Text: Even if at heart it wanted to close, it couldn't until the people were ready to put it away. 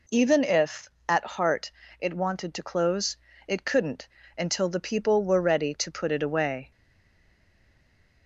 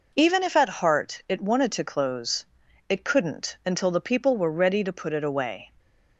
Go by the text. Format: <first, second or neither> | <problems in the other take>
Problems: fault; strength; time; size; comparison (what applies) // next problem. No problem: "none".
second | pauses between "heart" and "it"; slight; at 1.7 s; 0.26 s long // pauses between "couldn't" and "until"; slight; at 4.0 s; 0.32 s long // stays silent after the last word; noticeable; from 6.7 s on; 1.5 s long